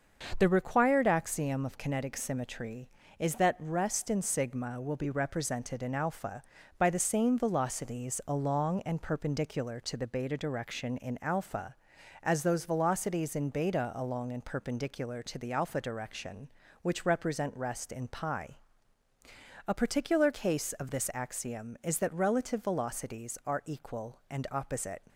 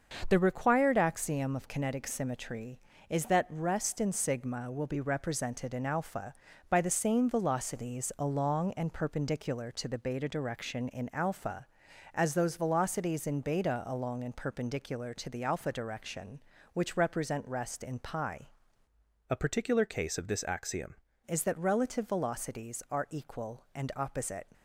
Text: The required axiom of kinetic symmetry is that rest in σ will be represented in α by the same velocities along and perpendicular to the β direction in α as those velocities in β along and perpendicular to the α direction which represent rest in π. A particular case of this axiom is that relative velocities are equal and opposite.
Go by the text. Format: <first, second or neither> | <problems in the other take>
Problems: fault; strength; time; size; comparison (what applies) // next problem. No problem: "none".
first | starts louder than the rest; until 1.2 s; 6.5 dB; also in the first // changes voice from "A" to "axiom"; from 19.2 to 20.9 s; 1.7 s long